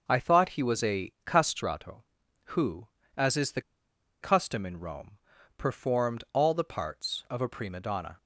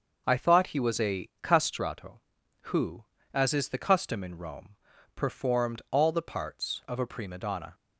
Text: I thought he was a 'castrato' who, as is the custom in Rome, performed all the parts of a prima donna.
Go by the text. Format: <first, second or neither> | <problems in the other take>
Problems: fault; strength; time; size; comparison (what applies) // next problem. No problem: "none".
second | starts louder than the rest; noticeable; until 1.0 s; 6 dB; noticeable in the second // pauses between "the" and "custom"; noticeable; at 3.6 s; 0.61 s long